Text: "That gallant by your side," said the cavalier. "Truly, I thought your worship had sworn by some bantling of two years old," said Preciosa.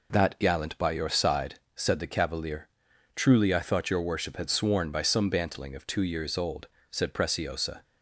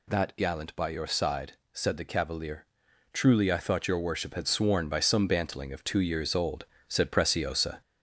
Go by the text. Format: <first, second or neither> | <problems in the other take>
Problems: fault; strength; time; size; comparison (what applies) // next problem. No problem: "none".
first | gets louder; throughout; 3.5 dB